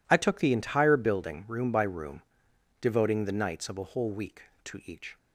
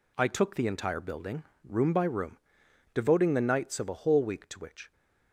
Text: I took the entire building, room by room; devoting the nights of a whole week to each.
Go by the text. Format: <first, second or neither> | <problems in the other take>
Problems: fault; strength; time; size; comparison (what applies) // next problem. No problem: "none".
first | says "which" for "each"; at 4.5 s